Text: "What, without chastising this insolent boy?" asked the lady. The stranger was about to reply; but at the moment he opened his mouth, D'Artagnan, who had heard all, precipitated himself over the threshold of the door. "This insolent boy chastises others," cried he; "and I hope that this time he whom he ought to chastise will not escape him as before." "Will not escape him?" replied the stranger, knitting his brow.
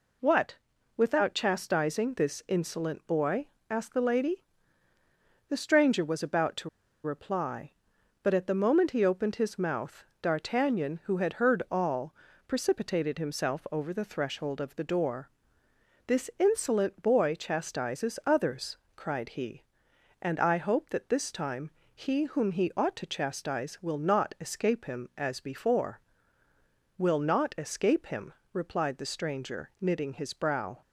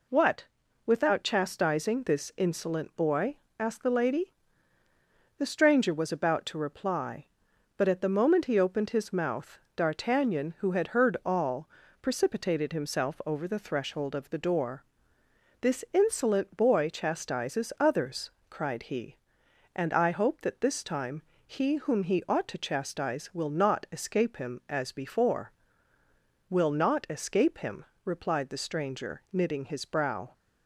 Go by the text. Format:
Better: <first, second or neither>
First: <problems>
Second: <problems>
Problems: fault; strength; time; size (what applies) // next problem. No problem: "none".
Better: second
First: pauses between "to" and "reply"; slight; at 6.6 s; 0.34 s long // pauses between "time" and "he"; slight; at 21.7 s; 0.20 s long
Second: pauses between "time" and "he"; slight; at 21.2 s; 0.20 s long